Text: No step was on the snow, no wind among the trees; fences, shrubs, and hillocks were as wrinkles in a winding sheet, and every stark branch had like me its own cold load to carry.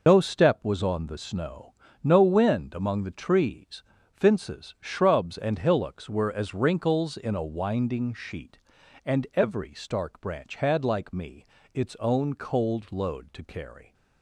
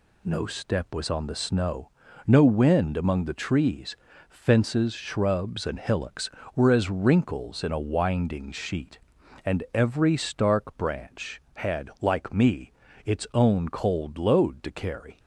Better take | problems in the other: second | loses the start of "No"; at 0.0 s; 80 ms // pauses between "me" and "its"; slight; at 11.4 s; 0.28 s long; slight in the second

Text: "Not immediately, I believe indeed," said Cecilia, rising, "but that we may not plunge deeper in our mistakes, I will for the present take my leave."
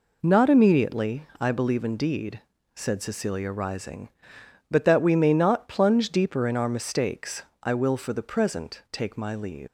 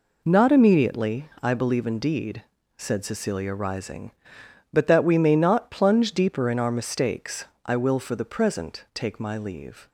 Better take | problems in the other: second | leaves "leave" unfinished; at 9.6 s; 185 ms

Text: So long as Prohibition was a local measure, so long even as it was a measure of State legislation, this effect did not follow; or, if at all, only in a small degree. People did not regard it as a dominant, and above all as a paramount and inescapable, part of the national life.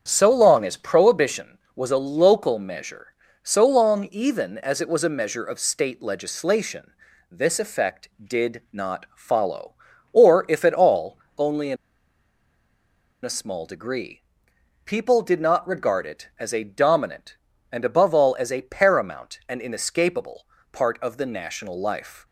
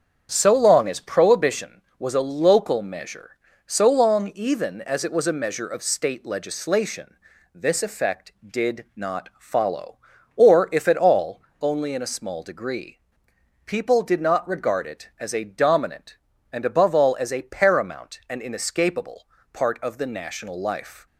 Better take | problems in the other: second | starts louder than the rest; strong; until 1.0 s; 7.5 dB; strong in the second // pauses between "in" and "a"; strong; at 11.7 s; 1.4 s long

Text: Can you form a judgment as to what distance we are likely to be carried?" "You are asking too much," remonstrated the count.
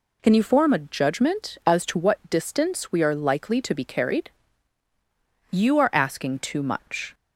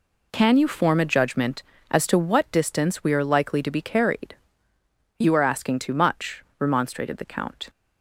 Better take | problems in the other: second | stops before "remonstrated the count"; at 7.1 s

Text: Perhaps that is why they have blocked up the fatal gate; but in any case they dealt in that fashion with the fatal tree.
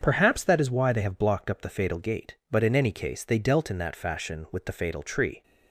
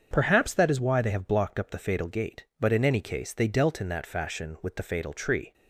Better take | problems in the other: neither | starts louder than the rest; strong; the same in both

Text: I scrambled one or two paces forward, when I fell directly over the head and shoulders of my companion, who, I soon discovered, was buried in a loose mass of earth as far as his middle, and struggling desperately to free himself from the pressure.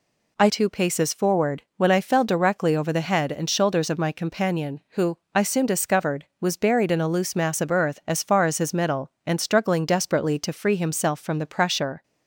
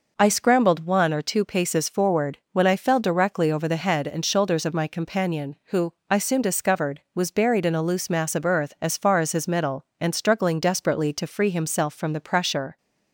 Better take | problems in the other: second | skips "scrambled one or"; at 0.4 s

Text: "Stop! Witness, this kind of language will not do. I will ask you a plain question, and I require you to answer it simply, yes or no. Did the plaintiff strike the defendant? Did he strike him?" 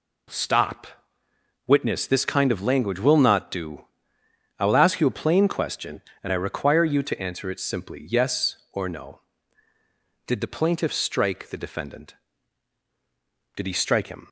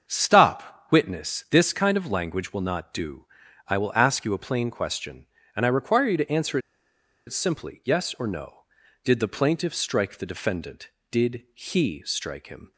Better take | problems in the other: first | starts louder than the rest; until 1.1 s; 7 dB // pauses between "answer" and "it"; noticeable; at 6.5 s; 0.68 s long

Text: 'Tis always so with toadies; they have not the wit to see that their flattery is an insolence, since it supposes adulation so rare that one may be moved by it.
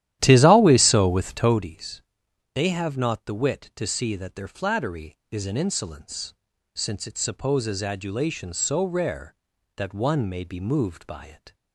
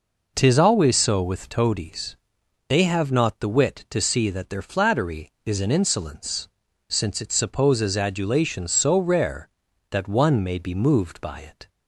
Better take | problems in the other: second | starts louder than the rest; strong; until 1.7 s; 12.5 dB

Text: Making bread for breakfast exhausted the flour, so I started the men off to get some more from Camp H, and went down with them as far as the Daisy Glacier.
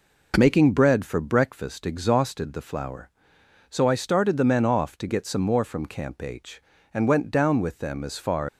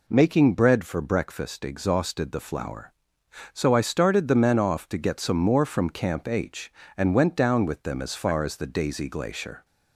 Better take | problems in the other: second | stops before "as the Daisy Glacier"; at 8.4 s

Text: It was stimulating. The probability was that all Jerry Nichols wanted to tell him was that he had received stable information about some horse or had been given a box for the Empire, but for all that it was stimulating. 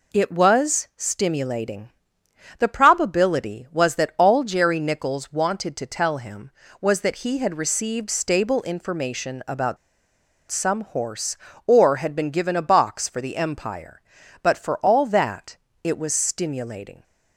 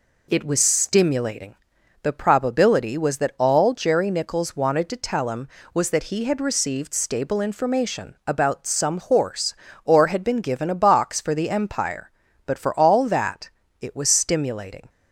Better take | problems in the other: second | pauses between "about" and "some"; noticeable; at 9.7 s; 0.73 s long // pauses between "that" and "it"; slight; at 15.5 s; 0.30 s long; slight in the second

